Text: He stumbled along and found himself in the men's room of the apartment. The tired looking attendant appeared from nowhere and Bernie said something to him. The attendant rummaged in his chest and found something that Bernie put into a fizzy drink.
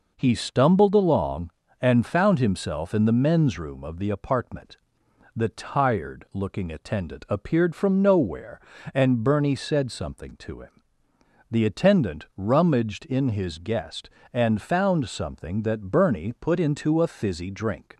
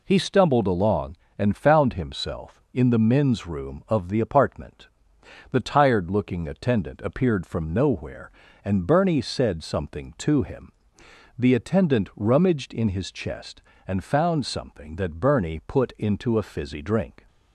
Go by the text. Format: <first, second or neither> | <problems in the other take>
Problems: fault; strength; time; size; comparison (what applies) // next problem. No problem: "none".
second | says "guest" for "chest"; at 13.5 s